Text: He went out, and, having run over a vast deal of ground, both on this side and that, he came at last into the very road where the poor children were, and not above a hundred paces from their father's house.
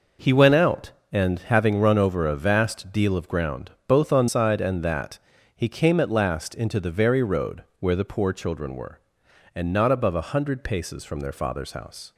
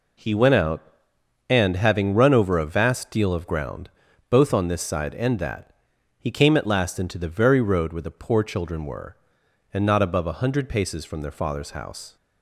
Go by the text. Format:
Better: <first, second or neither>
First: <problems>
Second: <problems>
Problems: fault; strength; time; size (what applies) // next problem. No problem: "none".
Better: second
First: skips "this"; at 4.2 s // pauses between "road" and "where"; slight; at 7.6 s; 0.16 s long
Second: none